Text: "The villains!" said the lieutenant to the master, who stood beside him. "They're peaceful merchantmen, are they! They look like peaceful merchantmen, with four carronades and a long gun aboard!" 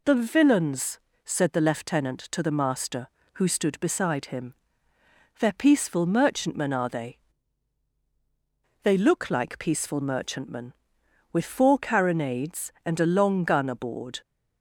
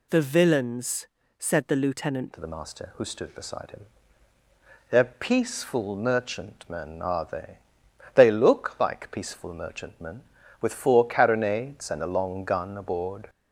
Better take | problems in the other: first | changes voice at "to"; from 2.3 s on; 10.9 s long

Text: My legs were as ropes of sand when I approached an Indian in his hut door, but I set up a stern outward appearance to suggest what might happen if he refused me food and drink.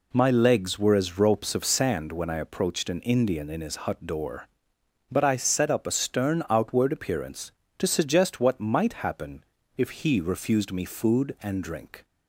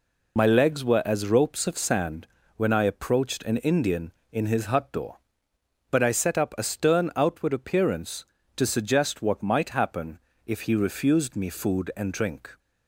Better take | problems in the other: first | loses the start of "My"; at 0.3 s; 55 ms // pauses between "sand" and "when"; slight; at 2.2 s; 0.30 s long // pauses between "happen" and "if"; slight; at 10.1 s; 0.26 s long; slight in the first

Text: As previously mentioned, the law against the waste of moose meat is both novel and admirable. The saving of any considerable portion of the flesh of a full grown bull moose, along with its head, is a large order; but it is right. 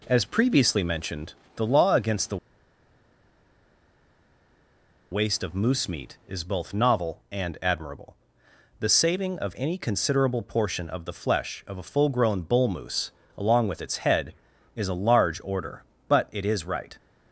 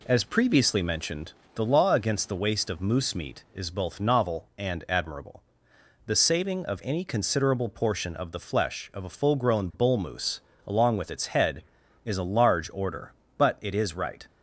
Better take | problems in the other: second | pauses between "the" and "waste"; strong; at 2.3 s; 2.7 s long

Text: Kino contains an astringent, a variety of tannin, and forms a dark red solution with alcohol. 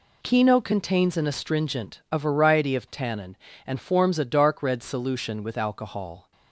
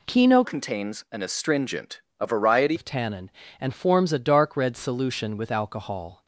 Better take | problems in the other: first | changes voice from "contains" to "variety"; from 0.4 to 2.7 s; 2.3 s long

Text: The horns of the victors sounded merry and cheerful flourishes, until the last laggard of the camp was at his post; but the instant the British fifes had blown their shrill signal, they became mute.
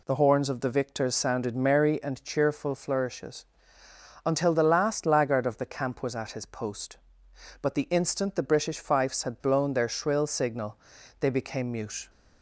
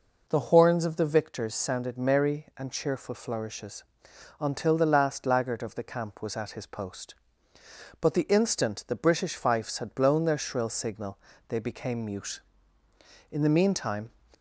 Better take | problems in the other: first | goes on to say "In the meantime"; noticeable; from 13.2 s on; 0.80 s long

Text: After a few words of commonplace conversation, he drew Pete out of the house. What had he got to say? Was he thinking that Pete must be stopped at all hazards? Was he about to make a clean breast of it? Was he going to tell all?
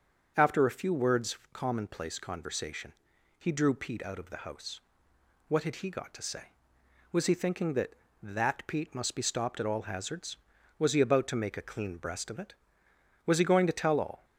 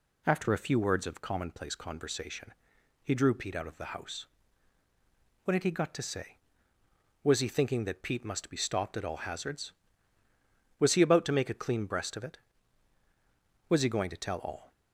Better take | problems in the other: second | starts louder than the rest; until 1.3 s; 7 dB // says "that" twice; at 8.2 s

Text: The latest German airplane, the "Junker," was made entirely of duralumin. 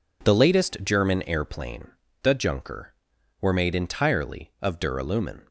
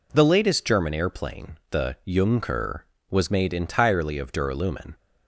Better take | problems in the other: second | says "were" for "was"; at 3.3 s

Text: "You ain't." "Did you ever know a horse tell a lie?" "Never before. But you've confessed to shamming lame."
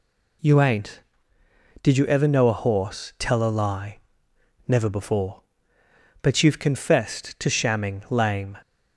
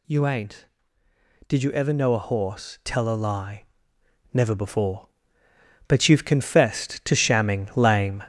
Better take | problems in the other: first | gets louder; noticeable; throughout; 4.5 dB

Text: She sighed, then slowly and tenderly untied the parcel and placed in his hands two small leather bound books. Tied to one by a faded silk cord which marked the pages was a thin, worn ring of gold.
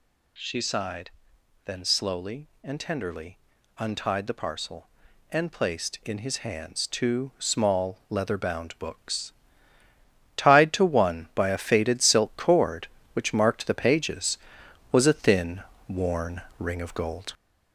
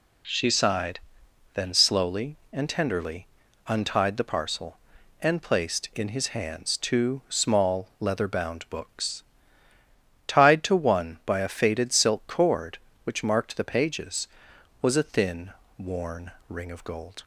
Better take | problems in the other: second | gets louder; throughout; 3.5 dB // pauses between "tenderly" and "untied"; at 3.3 s; 0.40 s long; also in the second // pauses between "worn" and "ring"; slight; at 16.4 s; 0.18 s long; slight in the second

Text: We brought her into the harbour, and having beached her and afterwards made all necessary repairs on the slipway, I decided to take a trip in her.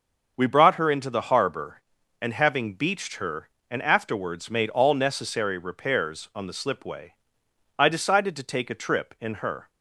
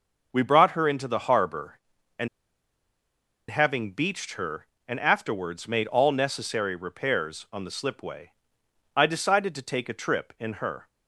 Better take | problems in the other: first | starts louder than the rest; until 1.3 s; 6.5 dB; also in the first // pauses between "and" and "having"; at 2.2 s; 1.2 s long

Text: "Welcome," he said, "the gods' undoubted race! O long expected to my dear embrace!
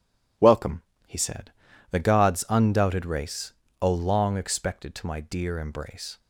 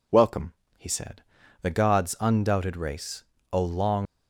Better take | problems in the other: first | stops before "expected to my dear embrace"; at 4.0 s

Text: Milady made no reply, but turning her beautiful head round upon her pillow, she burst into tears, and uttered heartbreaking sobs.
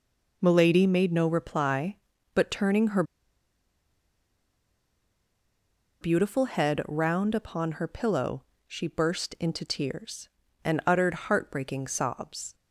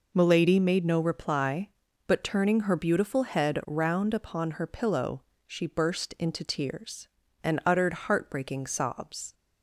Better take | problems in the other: second | pauses between "her" and "beautiful"; strong; at 3.0 s; 2.9 s long

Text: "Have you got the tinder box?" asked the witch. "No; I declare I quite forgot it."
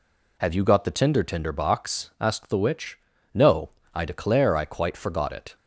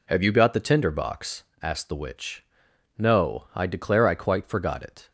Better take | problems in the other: second | says "tinder" twice; at 1.2 s

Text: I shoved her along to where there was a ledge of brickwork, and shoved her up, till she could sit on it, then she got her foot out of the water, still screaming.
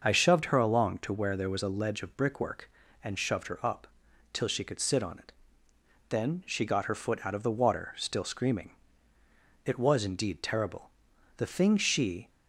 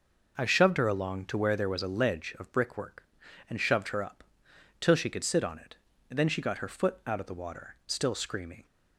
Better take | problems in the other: second | starts louder than the rest; until 1.0 s; 6 dB // goes on to say "It was indeed terrible The thing she"; strong; from 9.6 s on; 2.6 s long

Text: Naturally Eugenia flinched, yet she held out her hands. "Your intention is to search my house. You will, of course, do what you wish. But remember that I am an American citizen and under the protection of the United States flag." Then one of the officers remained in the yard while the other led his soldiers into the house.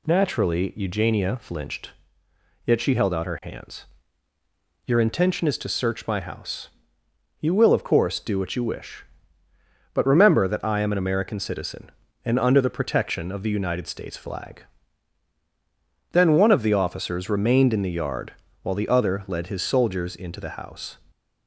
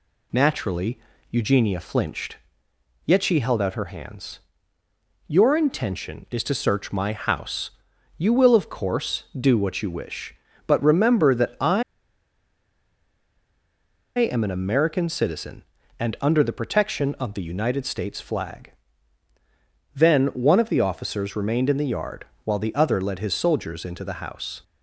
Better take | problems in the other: first | pauses between "Naturally" and "Eugenia"; slight; at 0.9 s; 0.32 s long // pauses between "I" and "am"; strong; at 11.8 s; 2.3 s long // pauses between "yard" and "while"; slight; at 22.2 s; 0.20 s long; slight in the first

